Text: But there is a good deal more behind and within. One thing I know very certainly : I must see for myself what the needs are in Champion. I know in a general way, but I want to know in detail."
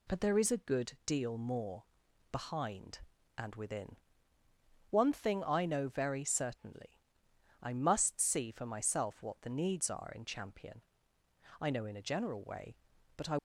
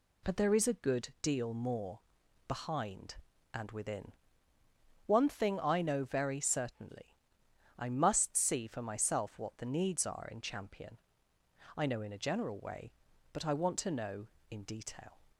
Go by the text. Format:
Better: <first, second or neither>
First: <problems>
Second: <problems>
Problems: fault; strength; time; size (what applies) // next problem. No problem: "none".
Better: second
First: pauses between "more" and "behind"; noticeable; at 1.8 s; 0.48 s long // stops before "want to know in detail"; at 13.3 s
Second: pauses between "more" and "behind"; noticeable; at 2.0 s; 0.48 s long